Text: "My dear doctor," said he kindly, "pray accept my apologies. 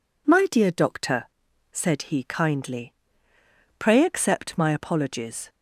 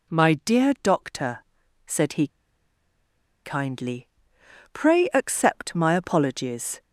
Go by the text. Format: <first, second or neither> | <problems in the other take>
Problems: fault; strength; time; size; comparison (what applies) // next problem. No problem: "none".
first | pauses between "he" and "kindly"; at 2.2 s; 1.1 s long